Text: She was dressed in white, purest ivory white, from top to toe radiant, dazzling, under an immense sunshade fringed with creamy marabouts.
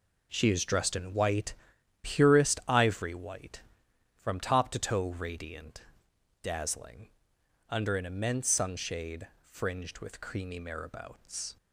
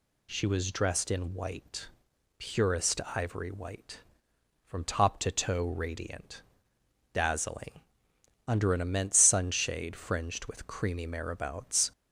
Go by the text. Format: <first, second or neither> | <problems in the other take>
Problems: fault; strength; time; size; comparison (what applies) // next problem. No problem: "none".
second | says "is" for "was"; at 0.4 s // pauses between "sunshade" and "fringed"; slight; at 9.2 s; 0.16 s long